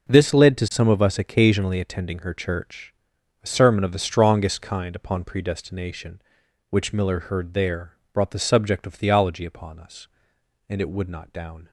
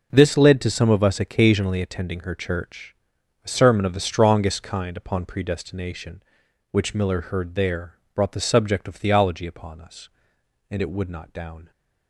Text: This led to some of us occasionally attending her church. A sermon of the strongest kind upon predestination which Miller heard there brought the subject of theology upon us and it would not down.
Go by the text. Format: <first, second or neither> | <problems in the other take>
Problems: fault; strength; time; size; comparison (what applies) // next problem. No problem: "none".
neither | pauses between "there" and "brought"; slight; the same in both